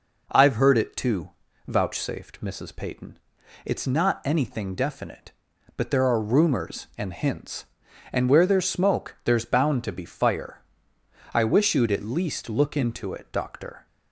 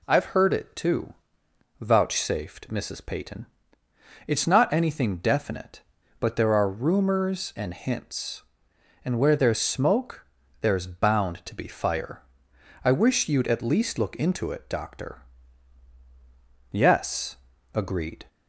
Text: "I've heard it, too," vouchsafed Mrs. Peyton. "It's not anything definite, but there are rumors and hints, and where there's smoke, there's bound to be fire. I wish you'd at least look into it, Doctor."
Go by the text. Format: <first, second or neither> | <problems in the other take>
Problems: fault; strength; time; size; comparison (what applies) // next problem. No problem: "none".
first | goes on to say "Yes agreed"; from 16.7 s on; 1.5 s long